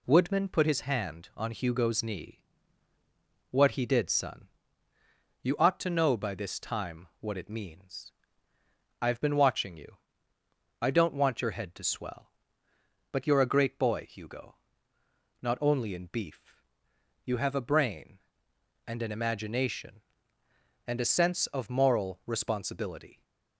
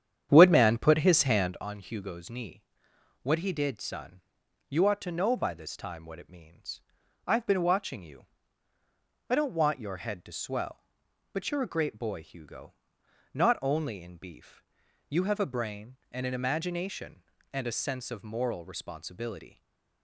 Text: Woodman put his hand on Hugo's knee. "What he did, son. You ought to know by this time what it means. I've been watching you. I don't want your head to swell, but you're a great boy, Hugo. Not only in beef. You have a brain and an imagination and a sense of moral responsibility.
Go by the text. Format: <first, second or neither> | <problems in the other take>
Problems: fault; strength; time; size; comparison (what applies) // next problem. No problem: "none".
first | starts louder than the rest; strong; until 1.6 s; 9 dB // stays silent after the last word; slight; from 19.4 s on; 0.6 s long